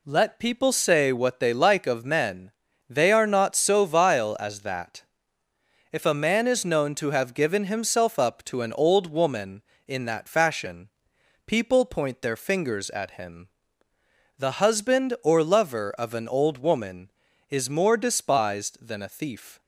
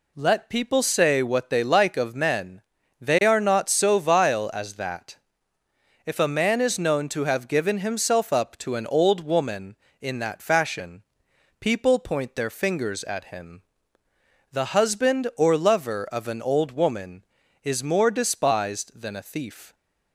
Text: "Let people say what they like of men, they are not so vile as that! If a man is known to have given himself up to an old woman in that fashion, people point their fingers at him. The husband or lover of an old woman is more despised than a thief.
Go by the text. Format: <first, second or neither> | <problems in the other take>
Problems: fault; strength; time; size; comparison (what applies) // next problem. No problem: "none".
neither | none